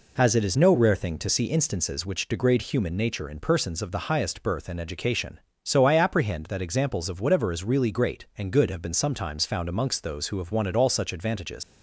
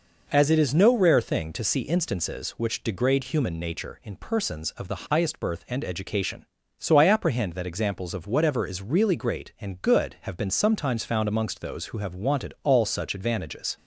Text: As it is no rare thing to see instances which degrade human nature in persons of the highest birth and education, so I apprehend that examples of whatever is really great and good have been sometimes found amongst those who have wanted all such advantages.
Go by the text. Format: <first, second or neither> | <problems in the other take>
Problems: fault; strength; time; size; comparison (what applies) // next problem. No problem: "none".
second | leaves "advantages" unfinished; at 11.6 s; 95 ms